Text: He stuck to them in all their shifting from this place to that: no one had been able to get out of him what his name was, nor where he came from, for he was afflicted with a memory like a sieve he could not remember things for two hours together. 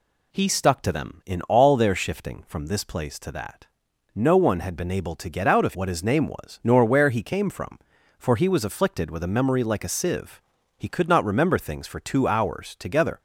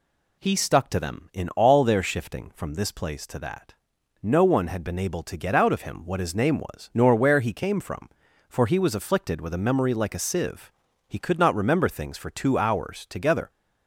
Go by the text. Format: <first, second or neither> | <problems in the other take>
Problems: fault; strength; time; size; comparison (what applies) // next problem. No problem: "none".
second | skips "him"; at 5.7 s // pauses between "sieve" and "he"; slight; at 10.4 s; 0.36 s long; slight in the second